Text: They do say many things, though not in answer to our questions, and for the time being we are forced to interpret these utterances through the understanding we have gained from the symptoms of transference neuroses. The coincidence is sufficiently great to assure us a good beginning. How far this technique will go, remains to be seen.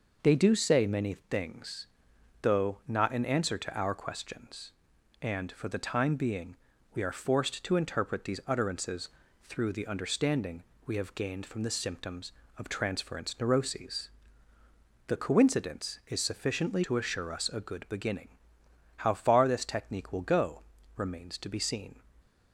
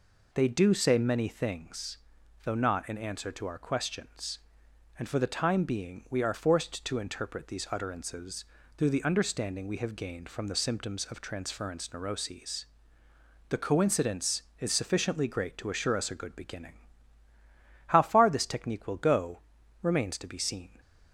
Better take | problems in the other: second | pauses between "being" and "we"; at 6.5 s; 0.38 s long // pauses between "utterances" and "through"; slight; at 9.0 s; 0.34 s long; slight in the second // pauses between "understanding" and "we"; slight; at 10.6 s; 0.22 s long // skips "great"; at 16.8 s

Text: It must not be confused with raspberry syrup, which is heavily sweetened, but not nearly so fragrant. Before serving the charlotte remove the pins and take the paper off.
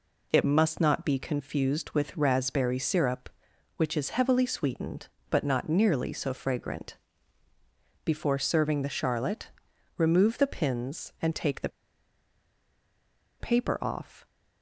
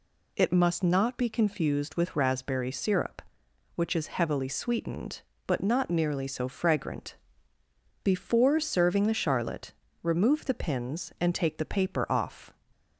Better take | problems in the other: second | pauses between "charlotte" and "remove"; noticeable; at 9.4 s; 0.48 s long; slight in the second // pauses between "the" and "paper"; strong; at 11.6 s; 1.7 s long

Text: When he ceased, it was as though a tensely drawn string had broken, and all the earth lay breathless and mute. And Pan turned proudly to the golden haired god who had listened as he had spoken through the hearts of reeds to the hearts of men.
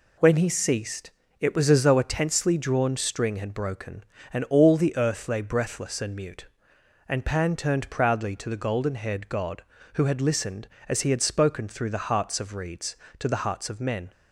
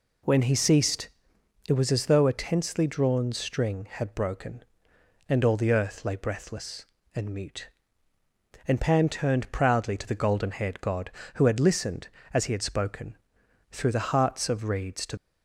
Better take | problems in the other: first | pauses between "spoken" and "through"; noticeable; at 13.1 s; 0.52 s long // stops before "the hearts of men"; at 15.1 s

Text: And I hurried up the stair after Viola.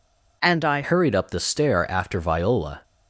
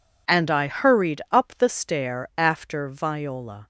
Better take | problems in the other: second | changes voice at "hurried"; from 0.8 s on; 2.0 s long

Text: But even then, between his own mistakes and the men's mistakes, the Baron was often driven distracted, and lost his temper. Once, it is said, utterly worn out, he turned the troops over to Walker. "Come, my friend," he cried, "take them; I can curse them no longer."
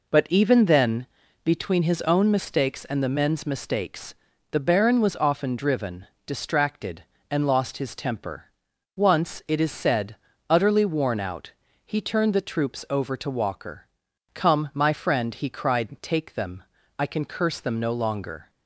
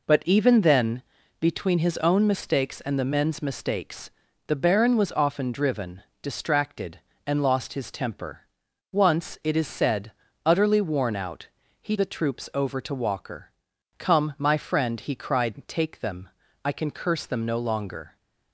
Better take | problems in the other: first | pauses between "driven" and "distracted"; slight; at 6.0 s; 0.20 s long; slight in the first // skips "turned"; at 11.9 s

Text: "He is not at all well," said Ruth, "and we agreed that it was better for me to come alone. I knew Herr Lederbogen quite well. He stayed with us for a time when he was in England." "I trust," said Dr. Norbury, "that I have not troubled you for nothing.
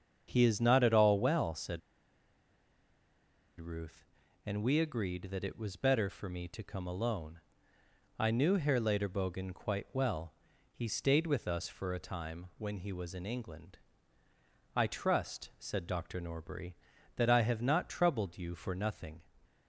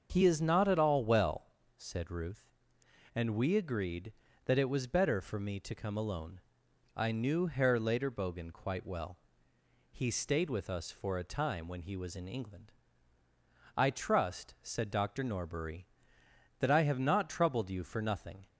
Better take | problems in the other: second | starts louder than the rest; strong; until 1.2 s; 7.5 dB; also in the second // pauses between "said" and "Ruth"; strong; at 1.8 s; 1.8 s long

